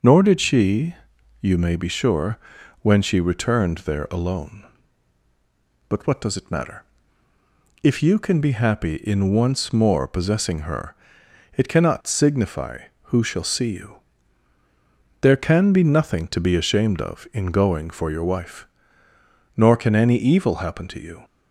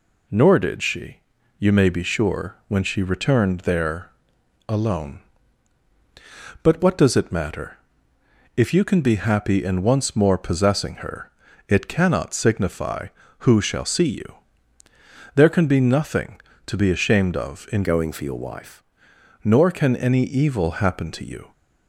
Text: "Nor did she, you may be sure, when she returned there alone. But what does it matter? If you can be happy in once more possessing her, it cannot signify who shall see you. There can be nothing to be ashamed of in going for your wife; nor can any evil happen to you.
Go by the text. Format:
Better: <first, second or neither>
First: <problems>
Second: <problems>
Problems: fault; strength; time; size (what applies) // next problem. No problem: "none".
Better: first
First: none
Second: pauses between "there" and "alone"; noticeable; at 4.1 s; 0.56 s long // changes voice from "going" to "wife"; from 17.8 to 18.8 s; 1.0 s long